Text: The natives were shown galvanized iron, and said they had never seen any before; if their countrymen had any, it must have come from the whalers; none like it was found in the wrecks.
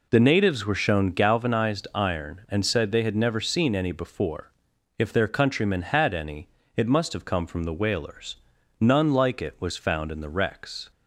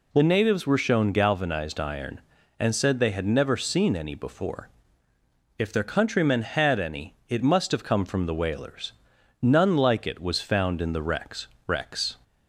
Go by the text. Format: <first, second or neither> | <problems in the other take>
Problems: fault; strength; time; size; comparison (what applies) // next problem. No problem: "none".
first | says "wrecks" twice; at 11.6 s